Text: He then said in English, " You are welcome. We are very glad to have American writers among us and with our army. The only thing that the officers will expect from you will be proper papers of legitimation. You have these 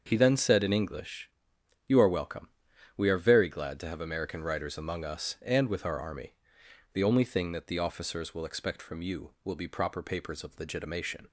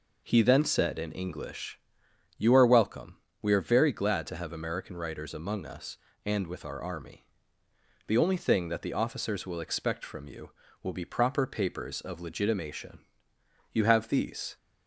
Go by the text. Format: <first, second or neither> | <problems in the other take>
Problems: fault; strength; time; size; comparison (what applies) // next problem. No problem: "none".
second | starts louder than the rest; until 1.0 s; 6.5 dB // stops before "You have these"; at 11.2 s